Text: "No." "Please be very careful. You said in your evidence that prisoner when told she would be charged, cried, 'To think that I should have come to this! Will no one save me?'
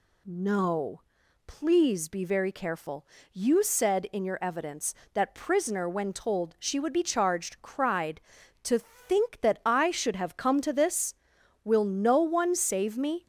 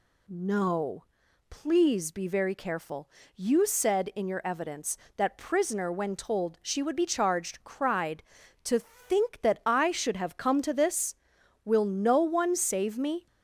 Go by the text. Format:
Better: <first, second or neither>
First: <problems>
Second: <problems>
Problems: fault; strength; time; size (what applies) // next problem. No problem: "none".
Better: neither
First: none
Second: none